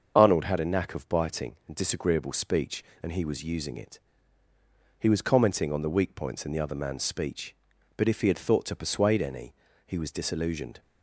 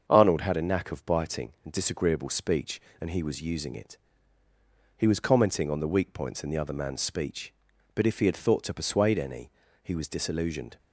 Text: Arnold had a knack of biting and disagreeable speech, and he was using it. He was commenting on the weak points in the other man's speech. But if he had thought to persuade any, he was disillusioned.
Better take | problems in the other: second | loses the start of "Arnold"; at 0.1 s; 35 ms // starts louder than the rest; until 1.1 s; 7 dB; also in the second

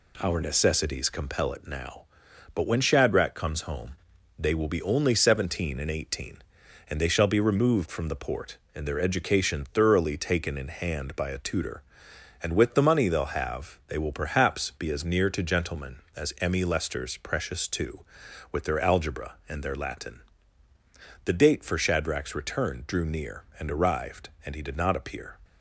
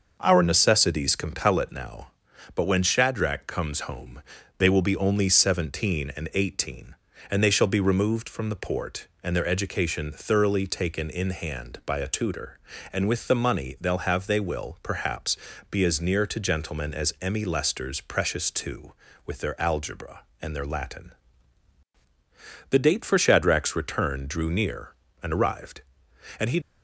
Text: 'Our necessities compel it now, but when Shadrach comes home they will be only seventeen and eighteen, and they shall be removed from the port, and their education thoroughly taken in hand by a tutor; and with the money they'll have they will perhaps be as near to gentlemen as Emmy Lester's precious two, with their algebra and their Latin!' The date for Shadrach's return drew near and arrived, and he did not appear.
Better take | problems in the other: first | pauses between "home" and "they"; at 4.2 s; 0.38 s long; also in the first // pauses between "perhaps" and "be"; slight; at 15.3 s; 0.32 s long // stops before "did not appear"; at 26.6 s

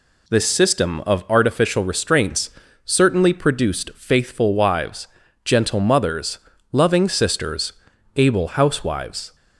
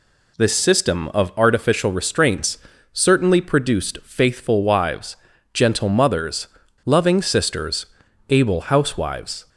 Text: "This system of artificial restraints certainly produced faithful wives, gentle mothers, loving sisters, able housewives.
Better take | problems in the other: neither | pauses between "restraints" and "certainly"; slight; the same in both

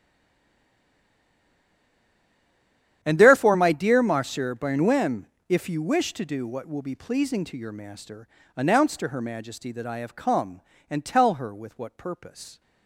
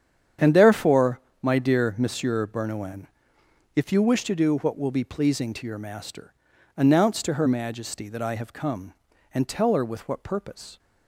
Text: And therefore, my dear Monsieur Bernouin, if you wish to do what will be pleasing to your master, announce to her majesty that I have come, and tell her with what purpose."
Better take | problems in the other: second | stays silent before the first word; strong; until 3.0 s; 3.0 s long // starts louder than the rest; strong; until 4.0 s; 10 dB; strong in the second

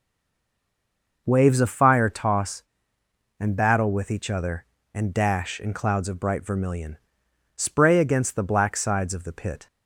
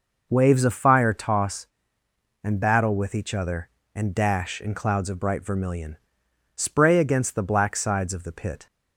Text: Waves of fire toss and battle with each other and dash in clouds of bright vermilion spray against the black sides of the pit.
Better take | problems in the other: second | stays silent before the first word; noticeable; until 1.2 s; 1.2 s long // pauses between "vermilion" and "spray"; noticeable; at 6.9 s; 0.58 s long; noticeable in the second

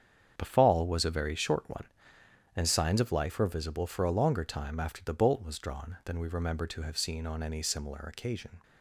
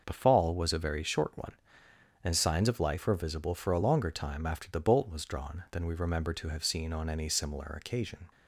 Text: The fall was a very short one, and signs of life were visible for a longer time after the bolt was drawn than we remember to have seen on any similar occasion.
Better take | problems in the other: second | gets quieter; strong; throughout; 10.5 dB // starts louder than the rest; strong; until 1.3 s; 8 dB; also in the second

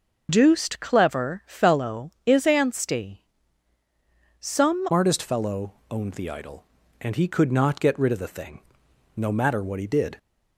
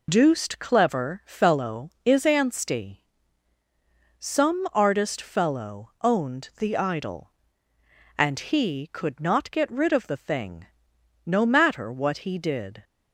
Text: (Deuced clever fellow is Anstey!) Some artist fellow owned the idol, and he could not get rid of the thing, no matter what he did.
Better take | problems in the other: second | changes voice at "artist"; from 4.9 s on; 5.2 s long

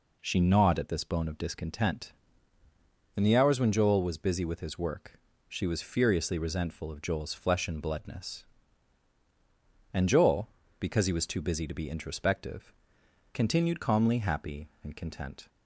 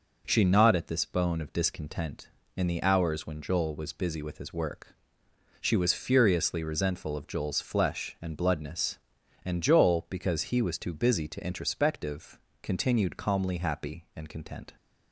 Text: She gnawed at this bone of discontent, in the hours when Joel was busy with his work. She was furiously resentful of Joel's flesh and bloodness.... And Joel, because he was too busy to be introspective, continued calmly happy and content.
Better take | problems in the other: first | skips "be"; at 11.4 s

